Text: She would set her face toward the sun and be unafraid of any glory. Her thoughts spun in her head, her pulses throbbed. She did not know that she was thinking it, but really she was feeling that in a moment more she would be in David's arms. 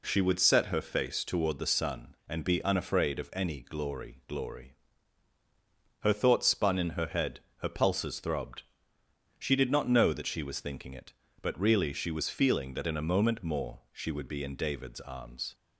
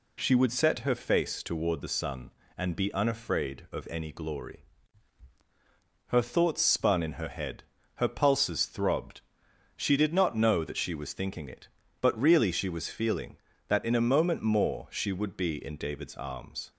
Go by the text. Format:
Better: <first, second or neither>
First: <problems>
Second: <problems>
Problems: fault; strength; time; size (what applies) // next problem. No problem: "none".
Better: second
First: says "glory" twice; at 4.2 s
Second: none